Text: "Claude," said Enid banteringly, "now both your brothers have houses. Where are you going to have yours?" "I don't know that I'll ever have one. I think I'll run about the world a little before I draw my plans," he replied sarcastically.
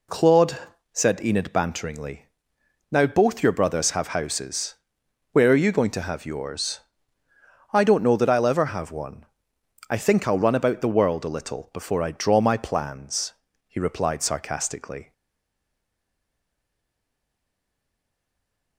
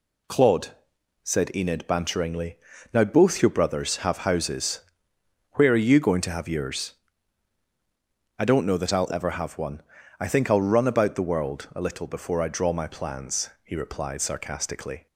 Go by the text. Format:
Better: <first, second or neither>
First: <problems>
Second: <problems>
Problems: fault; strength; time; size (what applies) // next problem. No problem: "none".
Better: second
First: stays silent after the last word; strong; from 15.1 s on; 3.6 s long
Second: none